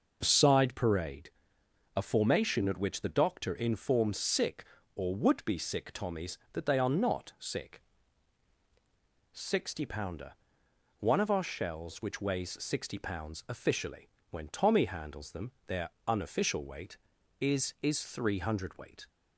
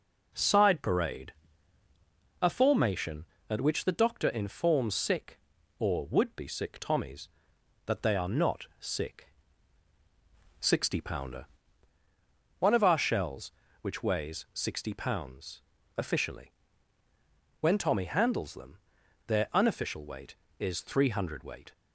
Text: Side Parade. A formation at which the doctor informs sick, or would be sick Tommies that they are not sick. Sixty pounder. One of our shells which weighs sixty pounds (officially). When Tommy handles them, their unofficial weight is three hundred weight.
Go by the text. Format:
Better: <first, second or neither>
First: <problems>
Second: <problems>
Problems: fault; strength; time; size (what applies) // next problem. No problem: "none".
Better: second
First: pauses between "their" and "unofficial"; slight; at 15.8 s; 0.16 s long // says "is" twice; at 17.8 s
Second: none